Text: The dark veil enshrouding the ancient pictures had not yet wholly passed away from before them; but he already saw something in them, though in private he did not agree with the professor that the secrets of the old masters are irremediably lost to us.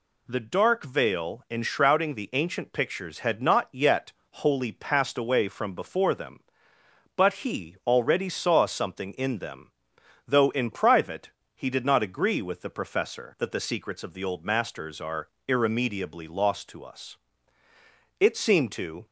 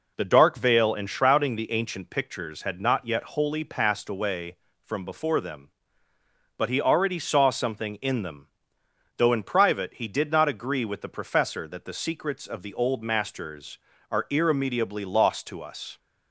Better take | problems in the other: second | pauses between "yet" and "wholly"; slight; at 4.1 s; 0.20 s long // pauses between "private" and "he"; slight; at 11.2 s; 0.26 s long // pauses between "are" and "irremediably"; slight; at 15.2 s; 0.18 s long // goes on to say "It seemed to"; noticeable; from 18.1 s on; 0.86 s long

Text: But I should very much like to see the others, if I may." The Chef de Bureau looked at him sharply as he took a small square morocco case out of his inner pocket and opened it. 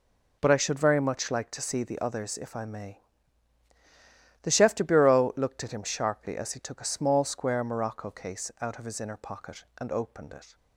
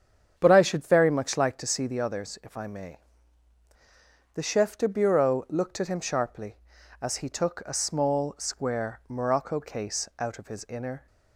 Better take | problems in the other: first | starts louder than the rest; strong; until 1.3 s; 8 dB // stops before "pocket and opened it"; at 11.0 s

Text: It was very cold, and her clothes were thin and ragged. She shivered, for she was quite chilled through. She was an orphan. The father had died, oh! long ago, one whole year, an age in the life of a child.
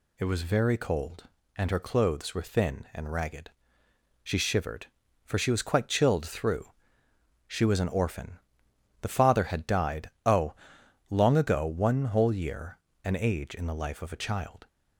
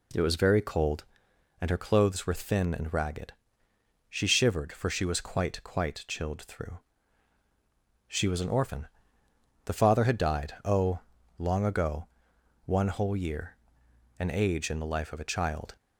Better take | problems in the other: first | says "quite" twice; at 5.6 s

